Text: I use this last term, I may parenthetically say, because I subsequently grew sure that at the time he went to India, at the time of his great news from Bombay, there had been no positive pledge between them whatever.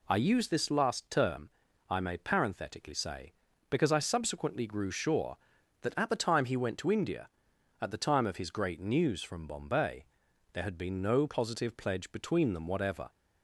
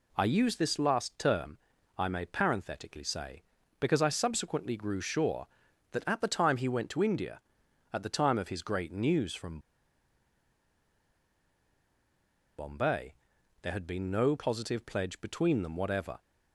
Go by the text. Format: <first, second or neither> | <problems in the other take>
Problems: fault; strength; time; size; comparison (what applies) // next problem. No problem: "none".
first | pauses between "from" and "Bombay"; strong; at 9.5 s; 2.9 s long